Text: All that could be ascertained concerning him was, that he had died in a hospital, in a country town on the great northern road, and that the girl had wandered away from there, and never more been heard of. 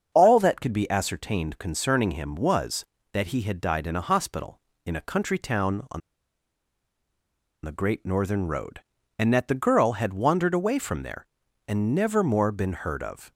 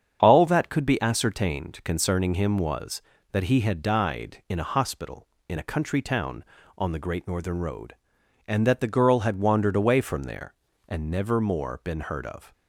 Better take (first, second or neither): second